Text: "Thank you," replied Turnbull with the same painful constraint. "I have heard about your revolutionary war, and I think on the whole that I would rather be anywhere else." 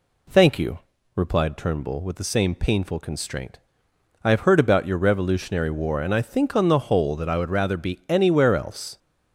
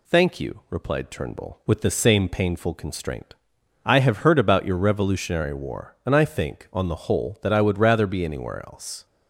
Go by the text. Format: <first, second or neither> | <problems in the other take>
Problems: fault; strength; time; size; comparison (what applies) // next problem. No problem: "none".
neither | none